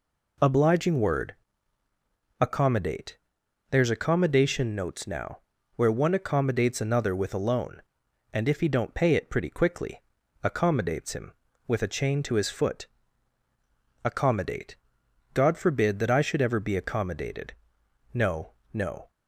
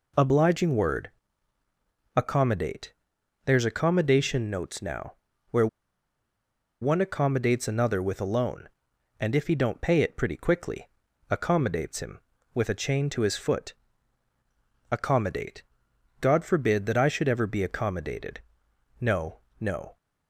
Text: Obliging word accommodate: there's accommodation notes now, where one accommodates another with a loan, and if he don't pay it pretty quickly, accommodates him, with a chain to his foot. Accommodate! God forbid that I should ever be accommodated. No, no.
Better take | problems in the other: first | pauses between "word" and "accommodate"; at 1.1 s; 1.0 s long; also in the first // pauses between "where" and "one"; at 5.6 s; 1.1 s long

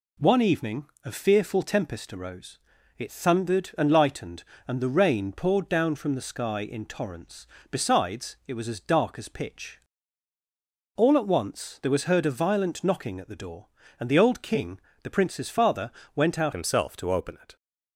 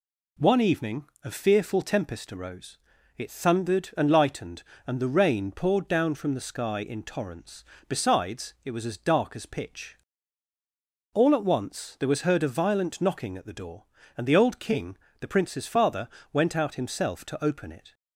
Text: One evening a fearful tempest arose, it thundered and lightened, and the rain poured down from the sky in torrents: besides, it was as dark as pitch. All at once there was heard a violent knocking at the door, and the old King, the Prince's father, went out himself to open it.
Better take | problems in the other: second | pauses between "evening" and "a"; slight; at 0.8 s; 0.18 s long; slight in the second // changes voice at "himself"; from 16.5 s on; 1.0 s long

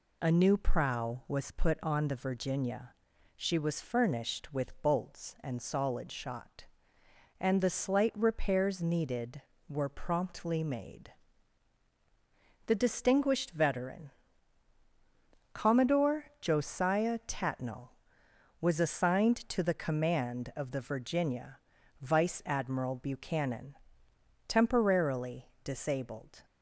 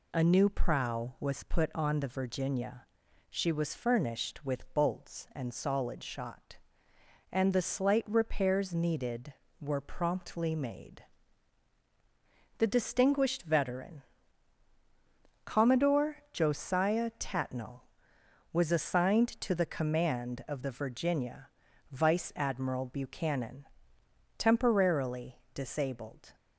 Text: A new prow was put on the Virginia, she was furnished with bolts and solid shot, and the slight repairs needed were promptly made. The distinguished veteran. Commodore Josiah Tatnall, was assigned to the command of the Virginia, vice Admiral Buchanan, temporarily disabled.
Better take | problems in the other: neither | pauses between "temporarily" and "disabled"; slight; the same in both

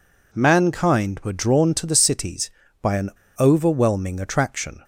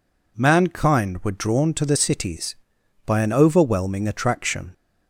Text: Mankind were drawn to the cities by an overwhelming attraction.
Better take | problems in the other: second | pauses between "an" and "overwhelming"; slight; at 3.0 s; 0.28 s long

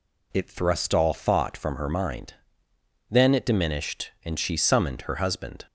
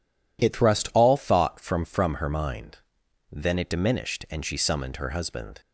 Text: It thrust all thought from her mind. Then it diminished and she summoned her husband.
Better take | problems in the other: first | says "from" twice; at 1.8 s

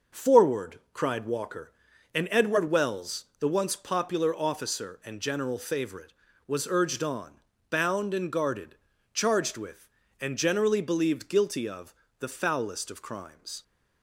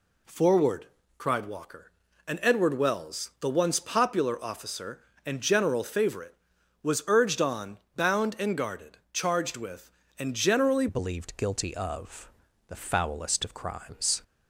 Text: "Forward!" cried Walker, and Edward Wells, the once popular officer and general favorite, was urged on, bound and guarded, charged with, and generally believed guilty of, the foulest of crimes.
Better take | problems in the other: first | changes voice at "believed"; from 10.8 s on; 3.4 s long

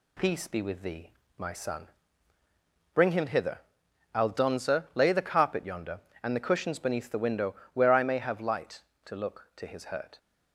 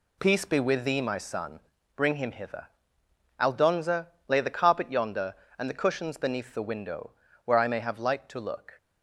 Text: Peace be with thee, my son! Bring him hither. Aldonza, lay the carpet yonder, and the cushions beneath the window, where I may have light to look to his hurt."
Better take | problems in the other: first | stops before "to his hurt"; at 8.7 s

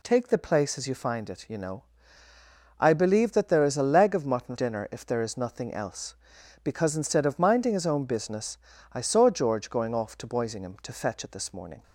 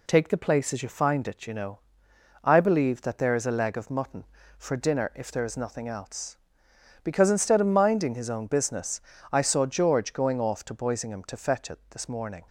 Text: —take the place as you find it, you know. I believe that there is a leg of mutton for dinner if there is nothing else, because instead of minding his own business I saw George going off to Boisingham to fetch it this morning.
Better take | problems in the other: second | skips "for"; at 4.5 s // pauses between "business" and "I"; at 8.5 s; 0.38 s long; slight in the second

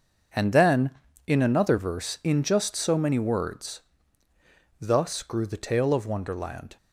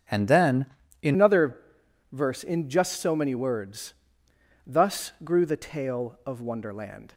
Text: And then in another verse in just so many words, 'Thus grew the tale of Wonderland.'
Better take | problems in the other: first | starts louder than the rest; strong; until 1.4 s; 7 dB; also in the first // changes voice at "another"; from 1.1 s on; 6.0 s long // pauses between "another" and "verse"; noticeable; at 1.5 s; 0.54 s long

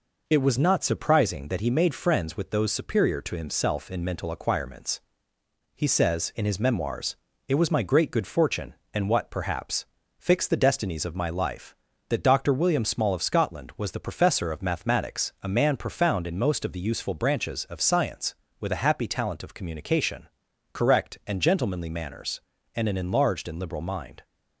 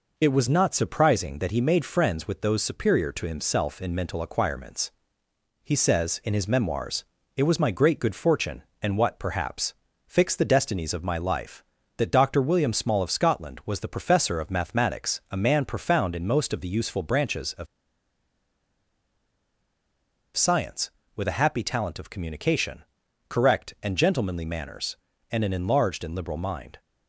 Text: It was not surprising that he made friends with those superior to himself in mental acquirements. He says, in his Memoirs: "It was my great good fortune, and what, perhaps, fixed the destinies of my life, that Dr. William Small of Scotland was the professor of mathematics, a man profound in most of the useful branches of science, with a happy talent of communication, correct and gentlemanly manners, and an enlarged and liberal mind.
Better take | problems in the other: first | pauses between "of" and "science"; strong; at 17.6 s; 2.6 s long

